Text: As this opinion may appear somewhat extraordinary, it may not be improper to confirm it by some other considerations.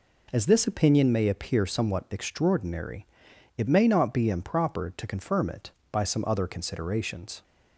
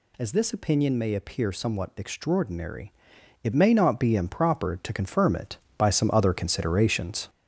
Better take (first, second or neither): first